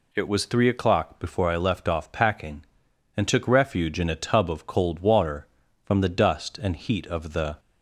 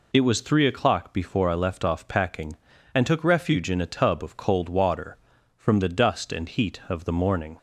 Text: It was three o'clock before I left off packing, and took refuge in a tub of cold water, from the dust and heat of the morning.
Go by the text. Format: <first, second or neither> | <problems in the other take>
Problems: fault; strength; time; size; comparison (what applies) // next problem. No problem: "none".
second | stops before "morning"; at 7.5 s